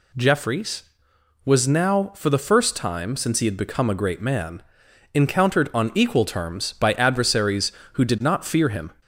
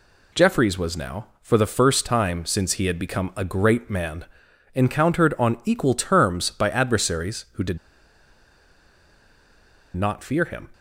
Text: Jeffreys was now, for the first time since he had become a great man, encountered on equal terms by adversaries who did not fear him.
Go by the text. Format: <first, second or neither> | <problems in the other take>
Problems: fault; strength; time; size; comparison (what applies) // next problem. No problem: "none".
first | pauses between "did" and "not"; strong; at 7.7 s; 2.1 s long